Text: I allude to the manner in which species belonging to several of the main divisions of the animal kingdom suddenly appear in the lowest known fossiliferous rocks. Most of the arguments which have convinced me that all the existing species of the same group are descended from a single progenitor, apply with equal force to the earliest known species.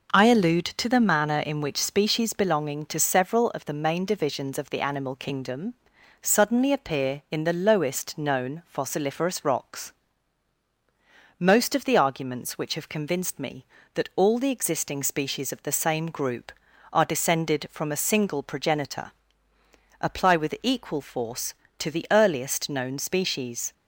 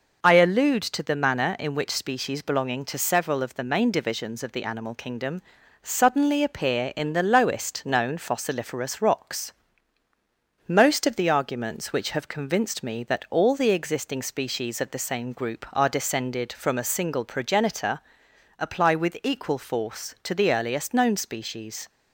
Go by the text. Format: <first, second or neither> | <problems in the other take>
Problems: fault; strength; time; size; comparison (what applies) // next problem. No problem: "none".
neither | pauses between "kingdom" and "suddenly"; the same in both